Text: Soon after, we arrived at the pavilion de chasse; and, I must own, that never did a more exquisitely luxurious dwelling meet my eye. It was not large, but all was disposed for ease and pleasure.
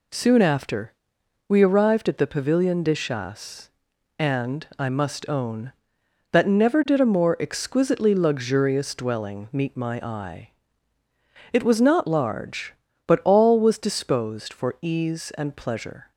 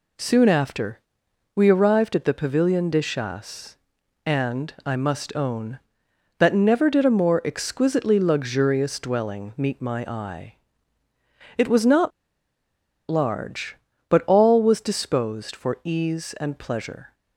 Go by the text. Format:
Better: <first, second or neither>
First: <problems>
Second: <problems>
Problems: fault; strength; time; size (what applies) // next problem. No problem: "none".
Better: first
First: none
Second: pauses between "not" and "large"; at 12.1 s; 0.99 s long